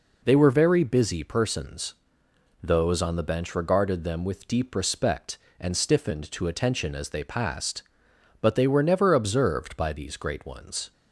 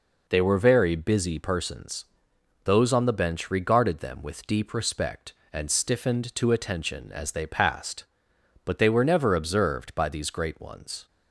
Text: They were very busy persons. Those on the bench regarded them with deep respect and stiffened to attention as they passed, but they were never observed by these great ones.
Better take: neither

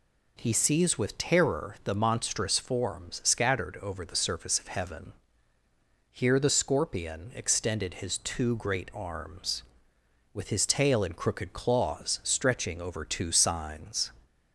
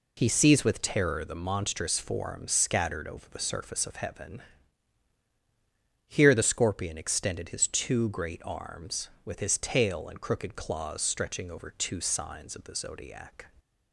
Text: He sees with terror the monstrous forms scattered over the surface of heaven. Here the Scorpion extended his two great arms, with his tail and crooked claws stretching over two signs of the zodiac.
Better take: second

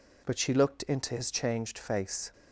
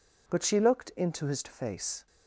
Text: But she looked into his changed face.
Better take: first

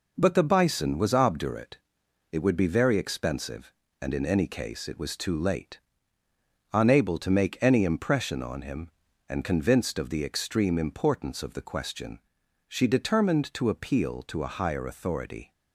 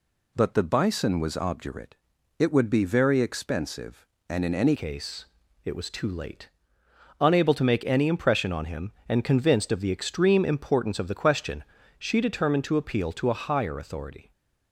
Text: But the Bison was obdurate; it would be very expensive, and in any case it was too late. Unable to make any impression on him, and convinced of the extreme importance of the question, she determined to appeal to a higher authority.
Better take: first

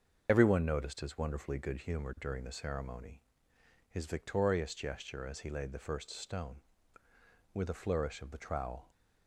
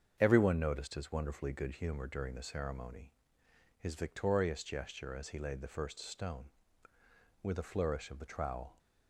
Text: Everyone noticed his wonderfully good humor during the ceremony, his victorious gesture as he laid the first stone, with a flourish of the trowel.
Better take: second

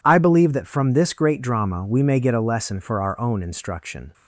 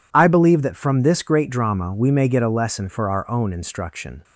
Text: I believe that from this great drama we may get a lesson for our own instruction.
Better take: neither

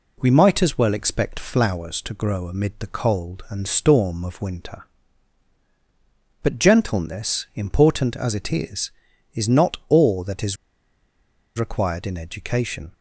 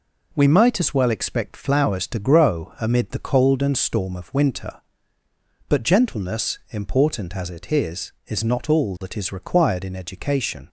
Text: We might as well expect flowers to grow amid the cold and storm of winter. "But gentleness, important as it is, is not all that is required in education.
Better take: second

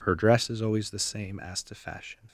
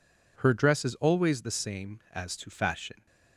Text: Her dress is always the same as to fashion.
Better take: neither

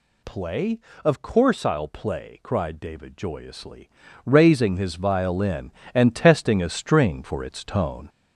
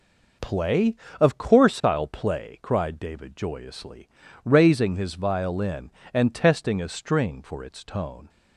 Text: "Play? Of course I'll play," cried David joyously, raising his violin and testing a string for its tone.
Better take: second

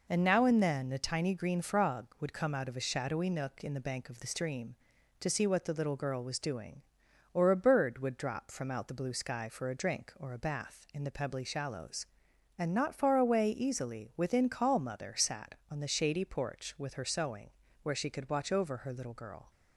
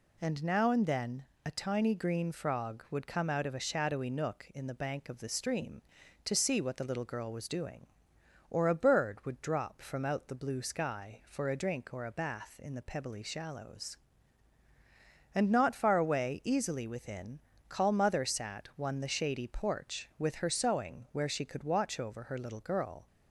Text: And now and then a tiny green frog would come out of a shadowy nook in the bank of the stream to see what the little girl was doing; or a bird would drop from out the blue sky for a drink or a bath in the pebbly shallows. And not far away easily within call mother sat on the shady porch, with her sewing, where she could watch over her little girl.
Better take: first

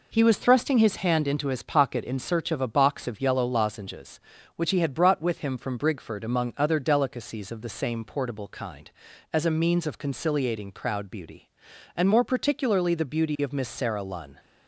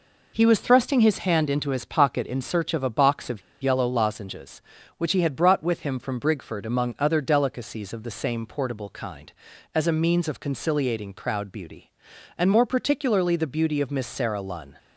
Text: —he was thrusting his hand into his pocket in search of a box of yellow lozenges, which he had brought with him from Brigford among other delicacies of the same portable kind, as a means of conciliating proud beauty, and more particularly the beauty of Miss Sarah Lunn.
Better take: first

